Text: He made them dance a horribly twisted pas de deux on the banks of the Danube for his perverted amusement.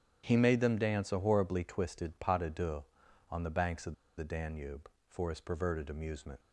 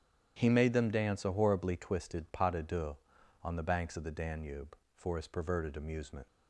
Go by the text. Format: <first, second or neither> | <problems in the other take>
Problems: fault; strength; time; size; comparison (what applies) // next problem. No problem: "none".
second | starts louder than the rest; strong; until 1.2 s; 9.5 dB; strong in the second // pauses between "of" and "the"; slight; at 3.9 s; 0.25 s long